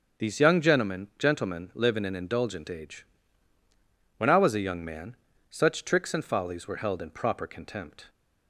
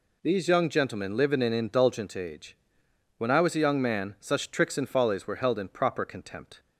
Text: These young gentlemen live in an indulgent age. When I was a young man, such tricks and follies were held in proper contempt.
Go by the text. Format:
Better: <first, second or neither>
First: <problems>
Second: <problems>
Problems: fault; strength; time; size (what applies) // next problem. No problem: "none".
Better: second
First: starts louder than the rest; until 1.3 s; 7 dB // says "gentlemen" twice; at 1.1 s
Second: none